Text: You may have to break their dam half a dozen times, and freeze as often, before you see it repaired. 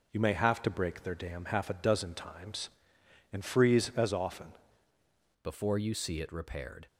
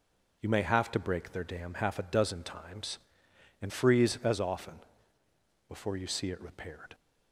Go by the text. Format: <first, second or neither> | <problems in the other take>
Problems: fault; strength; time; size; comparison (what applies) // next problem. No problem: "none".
second | changes voice at "before"; from 5.4 s on; 1.4 s long